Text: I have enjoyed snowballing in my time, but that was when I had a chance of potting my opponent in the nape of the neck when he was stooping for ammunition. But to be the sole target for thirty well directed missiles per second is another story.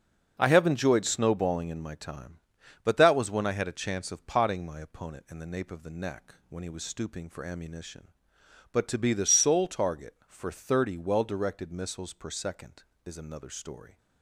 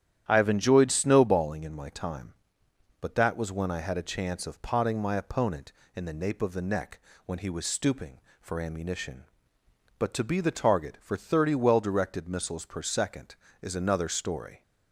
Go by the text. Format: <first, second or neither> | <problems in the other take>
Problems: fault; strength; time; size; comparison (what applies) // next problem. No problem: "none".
first | starts louder than the rest; strong; until 1.2 s; 10.5 dB; also in the first // pauses between "neck" and "when"; slight; at 6.9 s; 0.26 s long // skips "sole"; at 10.5 s